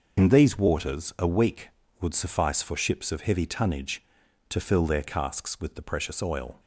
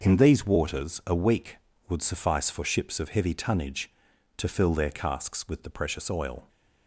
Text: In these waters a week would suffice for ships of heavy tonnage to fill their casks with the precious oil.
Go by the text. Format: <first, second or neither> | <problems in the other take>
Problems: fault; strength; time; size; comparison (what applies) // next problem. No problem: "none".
second | loses the start of "In"; at 0.1 s; 45 ms